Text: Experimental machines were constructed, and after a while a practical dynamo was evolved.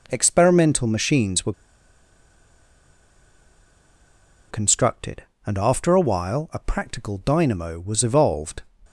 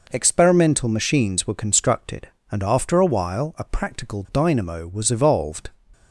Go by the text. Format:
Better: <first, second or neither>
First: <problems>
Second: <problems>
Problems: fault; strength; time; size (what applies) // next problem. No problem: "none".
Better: second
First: pauses between "were" and "constructed"; strong; at 1.5 s; 2.9 s long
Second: none